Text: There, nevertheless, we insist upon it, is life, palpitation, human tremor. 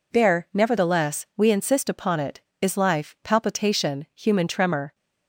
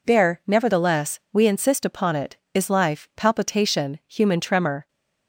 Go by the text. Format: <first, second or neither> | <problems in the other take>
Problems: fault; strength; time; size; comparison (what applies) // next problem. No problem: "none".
neither | none